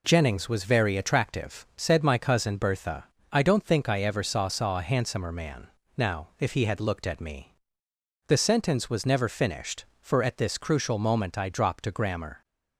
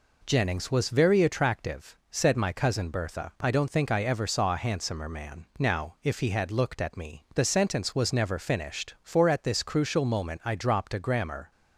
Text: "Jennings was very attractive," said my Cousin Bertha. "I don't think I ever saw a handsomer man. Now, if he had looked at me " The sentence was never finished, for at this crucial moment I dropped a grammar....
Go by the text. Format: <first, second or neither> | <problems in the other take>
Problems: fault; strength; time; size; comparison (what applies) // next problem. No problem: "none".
second | says "saw" twice; at 4.4 s